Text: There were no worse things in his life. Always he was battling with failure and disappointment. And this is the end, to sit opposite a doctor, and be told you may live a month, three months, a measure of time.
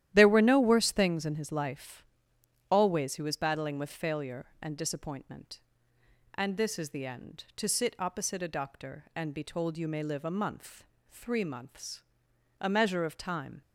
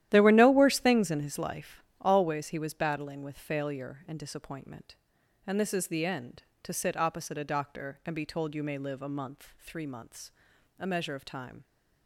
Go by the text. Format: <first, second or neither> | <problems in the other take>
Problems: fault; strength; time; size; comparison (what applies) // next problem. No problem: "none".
neither | starts louder than the rest; strong; the same in both